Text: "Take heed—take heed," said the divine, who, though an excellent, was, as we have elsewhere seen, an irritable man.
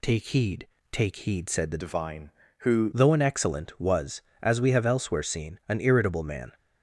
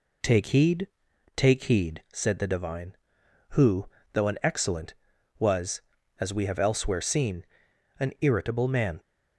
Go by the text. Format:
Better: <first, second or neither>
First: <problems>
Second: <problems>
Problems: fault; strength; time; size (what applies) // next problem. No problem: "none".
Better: second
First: changes voice from "divine" to "who"; from 1.8 to 2.9 s; 1.1 s long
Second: none